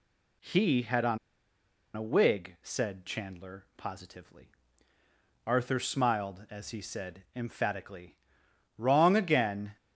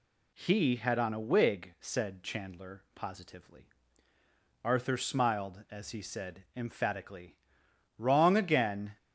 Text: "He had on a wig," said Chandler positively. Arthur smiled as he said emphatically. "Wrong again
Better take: second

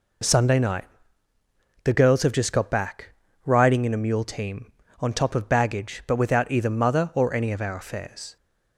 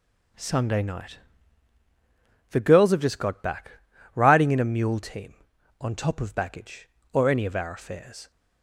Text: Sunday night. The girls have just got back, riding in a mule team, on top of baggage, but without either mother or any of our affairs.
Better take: first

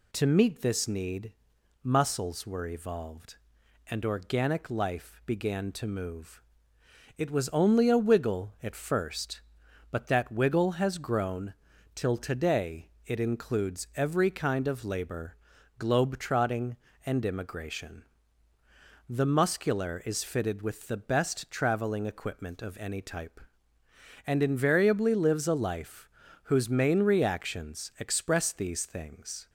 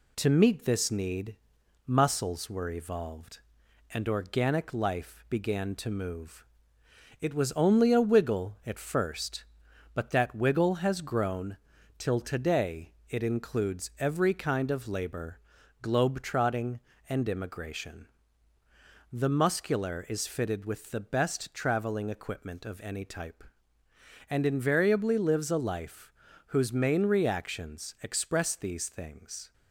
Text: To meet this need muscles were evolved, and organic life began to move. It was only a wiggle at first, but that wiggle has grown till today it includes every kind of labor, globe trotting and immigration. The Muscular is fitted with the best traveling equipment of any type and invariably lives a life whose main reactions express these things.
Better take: first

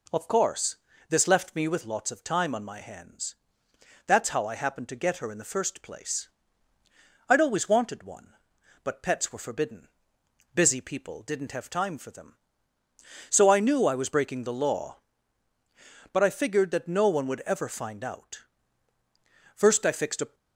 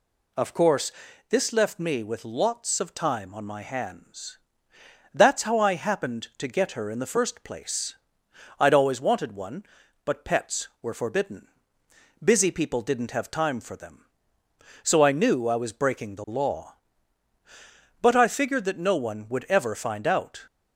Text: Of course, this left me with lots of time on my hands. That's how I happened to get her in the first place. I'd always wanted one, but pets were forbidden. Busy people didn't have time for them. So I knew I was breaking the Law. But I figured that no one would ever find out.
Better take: second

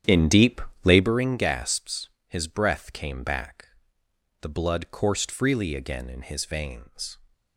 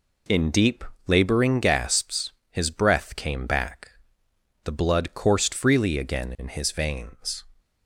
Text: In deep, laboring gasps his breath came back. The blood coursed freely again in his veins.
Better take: second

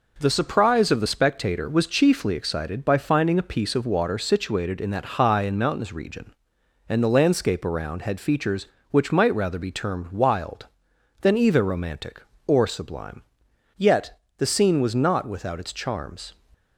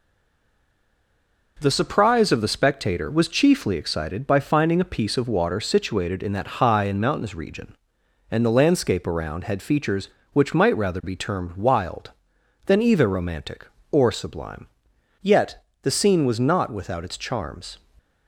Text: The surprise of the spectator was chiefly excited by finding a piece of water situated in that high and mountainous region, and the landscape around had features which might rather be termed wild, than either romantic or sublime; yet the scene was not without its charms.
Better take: first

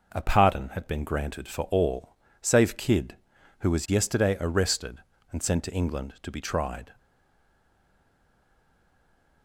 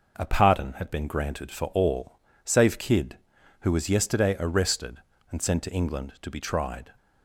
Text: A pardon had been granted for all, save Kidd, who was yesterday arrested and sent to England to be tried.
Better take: second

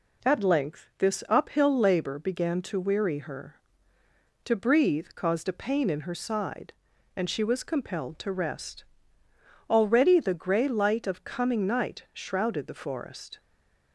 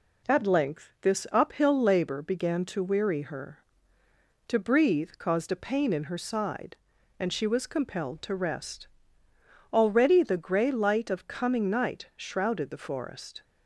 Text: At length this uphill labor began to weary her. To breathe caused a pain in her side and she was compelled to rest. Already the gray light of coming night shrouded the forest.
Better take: second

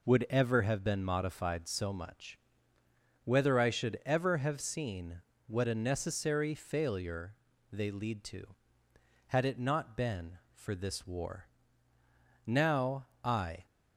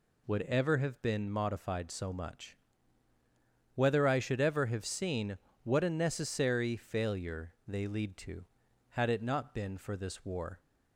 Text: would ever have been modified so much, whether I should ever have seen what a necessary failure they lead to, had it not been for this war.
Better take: second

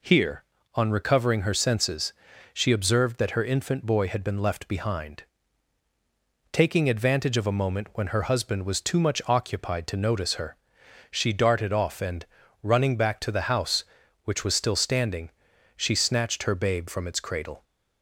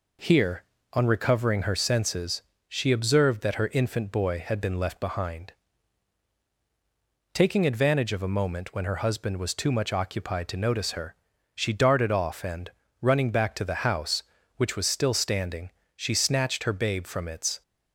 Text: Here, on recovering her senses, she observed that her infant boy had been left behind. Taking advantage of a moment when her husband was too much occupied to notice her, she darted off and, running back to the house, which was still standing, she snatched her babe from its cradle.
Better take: first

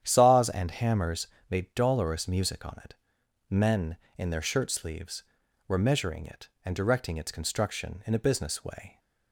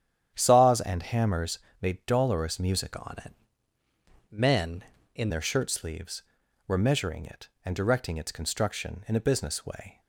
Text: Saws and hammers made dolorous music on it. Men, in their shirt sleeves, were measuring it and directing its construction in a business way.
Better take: first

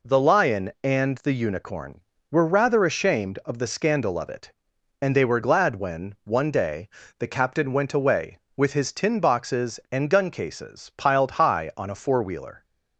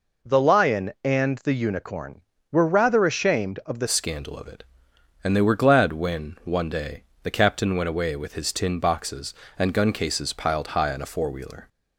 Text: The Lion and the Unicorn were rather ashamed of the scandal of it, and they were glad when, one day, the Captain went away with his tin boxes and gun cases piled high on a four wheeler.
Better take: first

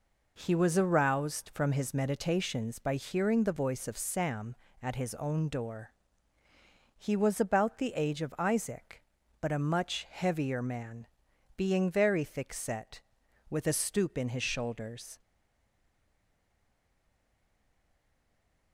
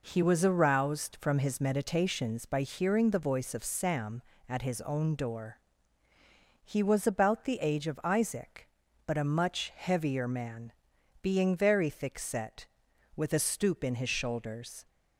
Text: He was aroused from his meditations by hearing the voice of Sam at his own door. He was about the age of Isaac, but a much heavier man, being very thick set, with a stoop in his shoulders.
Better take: second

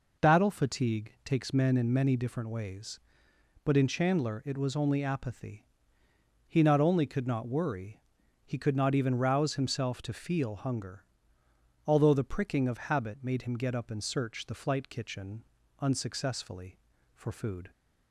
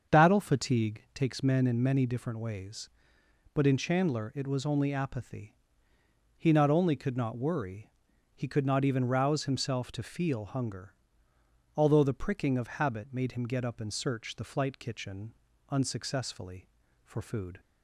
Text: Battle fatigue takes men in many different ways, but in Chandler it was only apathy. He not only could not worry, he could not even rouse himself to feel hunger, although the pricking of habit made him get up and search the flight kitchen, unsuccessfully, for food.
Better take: first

